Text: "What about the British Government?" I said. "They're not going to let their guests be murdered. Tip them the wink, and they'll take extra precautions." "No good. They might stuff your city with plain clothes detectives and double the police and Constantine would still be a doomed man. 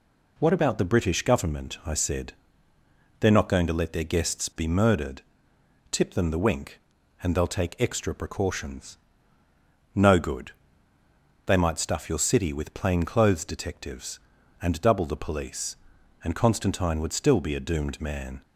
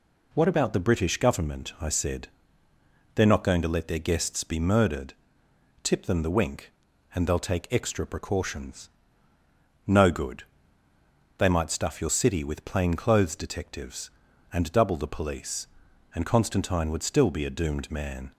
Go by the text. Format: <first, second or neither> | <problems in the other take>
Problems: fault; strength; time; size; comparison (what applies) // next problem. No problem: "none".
neither | none